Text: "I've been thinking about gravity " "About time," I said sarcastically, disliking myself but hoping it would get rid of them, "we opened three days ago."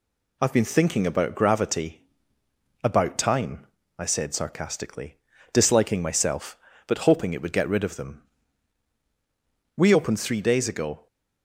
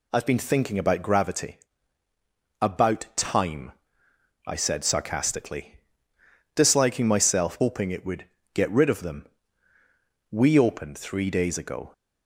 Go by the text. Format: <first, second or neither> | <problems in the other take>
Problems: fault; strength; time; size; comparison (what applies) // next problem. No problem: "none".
first | skips "but"; at 7.5 s // pauses between "would" and "get"; slight; at 8.2 s; 0.30 s long